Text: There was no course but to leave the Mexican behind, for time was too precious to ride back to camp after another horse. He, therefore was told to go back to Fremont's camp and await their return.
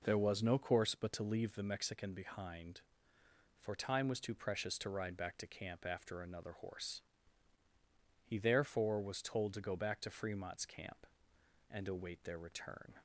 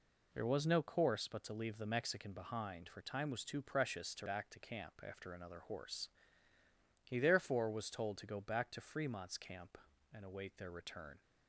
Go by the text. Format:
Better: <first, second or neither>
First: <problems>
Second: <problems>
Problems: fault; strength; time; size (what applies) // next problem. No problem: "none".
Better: first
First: none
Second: skips "ride"; at 4.2 s